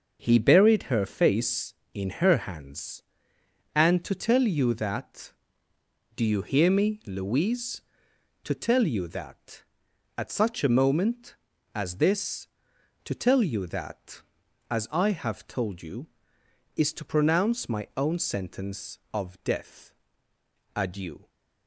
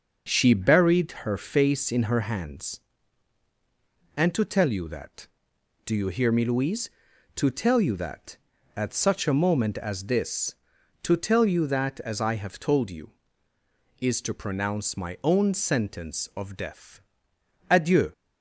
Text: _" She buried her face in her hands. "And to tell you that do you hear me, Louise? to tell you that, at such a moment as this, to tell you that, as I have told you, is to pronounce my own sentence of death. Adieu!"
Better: second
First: starts louder than the rest; until 1.3 s; 7 dB // says "He" for "She"; at 0.2 s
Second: starts louder than the rest; noticeable; until 1.2 s; 6 dB

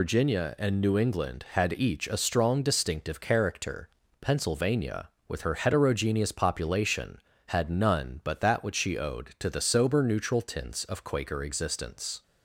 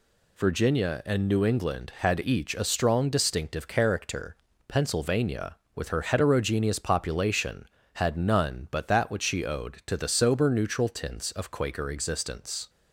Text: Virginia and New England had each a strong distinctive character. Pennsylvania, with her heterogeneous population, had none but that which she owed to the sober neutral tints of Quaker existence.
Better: second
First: loses the start of "Virginia"; at 0.0 s; 100 ms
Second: none

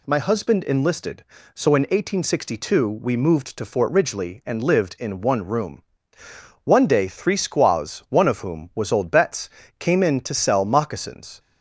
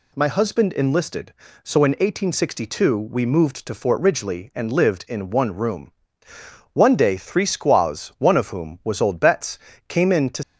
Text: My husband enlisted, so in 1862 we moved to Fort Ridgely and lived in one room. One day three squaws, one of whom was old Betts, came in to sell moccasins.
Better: first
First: none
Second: stops before "sell moccasins"; at 10.4 s

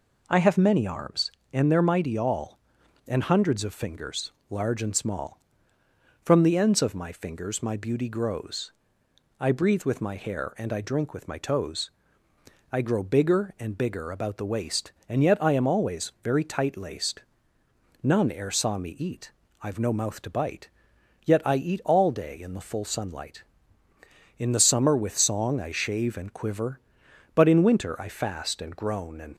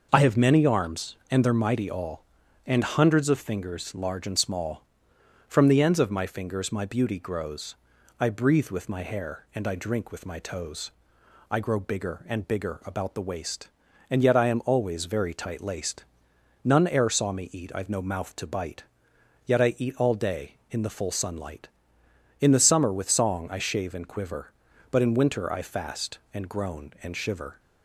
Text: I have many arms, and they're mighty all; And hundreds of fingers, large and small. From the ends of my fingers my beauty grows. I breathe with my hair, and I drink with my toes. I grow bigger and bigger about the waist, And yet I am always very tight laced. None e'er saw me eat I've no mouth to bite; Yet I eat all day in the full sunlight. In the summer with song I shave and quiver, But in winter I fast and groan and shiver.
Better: second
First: pauses between "eat" and "I've"; slight; at 19.3 s; 0.30 s long // stops before "shiver"; at 29.3 s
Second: none

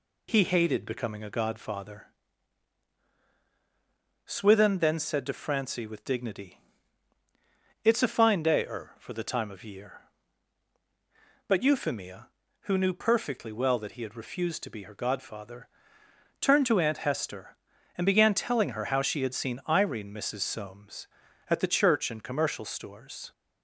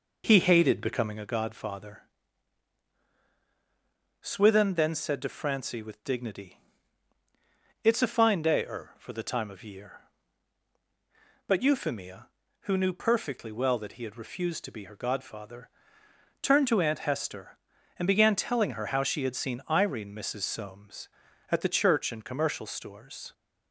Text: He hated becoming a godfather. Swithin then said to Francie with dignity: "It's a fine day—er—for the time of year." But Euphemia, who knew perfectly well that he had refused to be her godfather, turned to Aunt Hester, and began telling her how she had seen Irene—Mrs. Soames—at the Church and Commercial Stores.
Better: first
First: none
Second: starts louder than the rest; noticeable; until 1.3 s; 4.5 dB

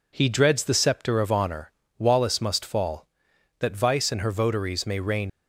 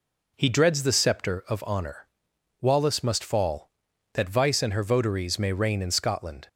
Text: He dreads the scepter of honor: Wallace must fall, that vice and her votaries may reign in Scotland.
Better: second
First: stops before "in Scotland"; at 5.2 s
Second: none

